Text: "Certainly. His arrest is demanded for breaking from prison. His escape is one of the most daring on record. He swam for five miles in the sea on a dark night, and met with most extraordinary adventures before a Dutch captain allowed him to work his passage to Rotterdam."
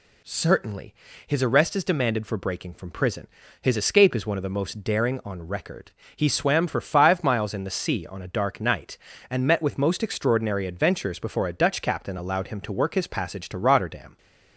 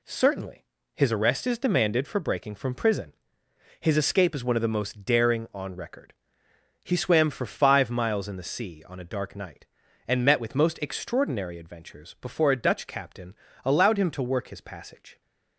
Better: first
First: none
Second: pauses between "captain" and "allowed"; slight; at 13.3 s; 0.30 s long // stops before "to Rotterdam"; at 15.2 s

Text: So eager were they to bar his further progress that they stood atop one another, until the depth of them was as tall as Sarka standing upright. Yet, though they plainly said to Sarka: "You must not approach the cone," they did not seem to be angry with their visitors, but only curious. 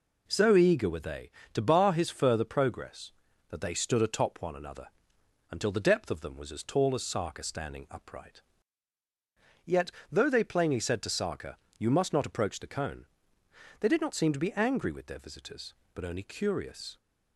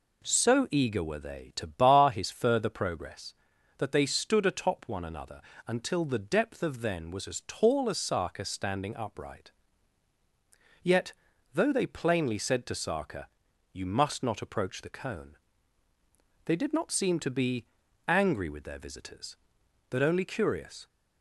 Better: first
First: none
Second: says "then" for "them"; at 6.8 s // pauses between "be" and "angry"; at 17.6 s; 0.42 s long

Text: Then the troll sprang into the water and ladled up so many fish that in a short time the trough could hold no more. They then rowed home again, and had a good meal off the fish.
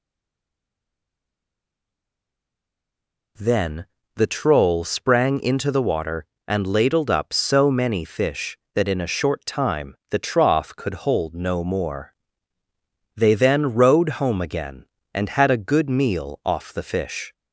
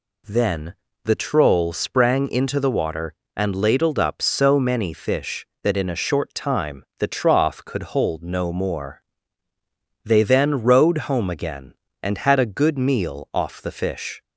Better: second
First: stays silent before the first word; strong; until 3.3 s; 3.3 s long // pauses between "Then" and "the"; slight; at 3.8 s; 0.30 s long // pauses between "time" and "the"; slight; at 9.9 s; 0.16 s long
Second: pauses between "Then" and "the"; slight; at 0.7 s; 0.30 s long // pauses between "time" and "the"; slight; at 6.8 s; 0.16 s long

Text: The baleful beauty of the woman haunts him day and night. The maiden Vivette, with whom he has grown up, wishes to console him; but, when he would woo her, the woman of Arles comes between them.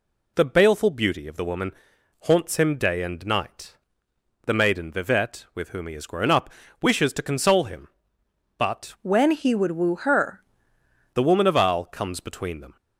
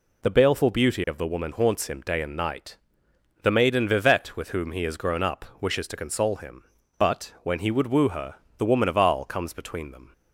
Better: second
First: pauses between "woman" and "haunts"; noticeable; at 1.7 s; 0.52 s long // changes voice from "when" to "her"; from 9.0 to 10.4 s; 1.4 s long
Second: none

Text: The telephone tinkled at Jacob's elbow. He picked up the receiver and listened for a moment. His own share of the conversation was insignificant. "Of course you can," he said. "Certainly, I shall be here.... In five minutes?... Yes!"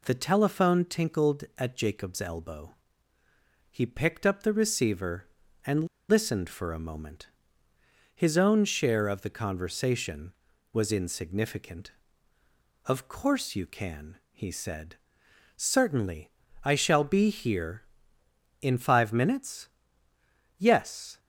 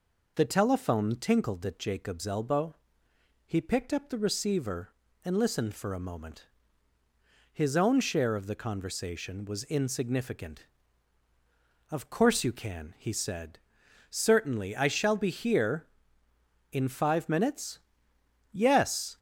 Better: second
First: pauses between "and" and "listened"; slight; at 5.8 s; 0.21 s long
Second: none

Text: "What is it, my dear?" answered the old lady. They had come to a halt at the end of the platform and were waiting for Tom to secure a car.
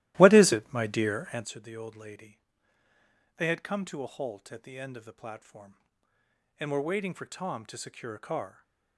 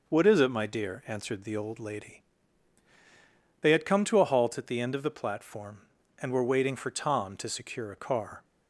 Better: second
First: starts louder than the rest; strong; until 1.5 s; 15.5 dB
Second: none

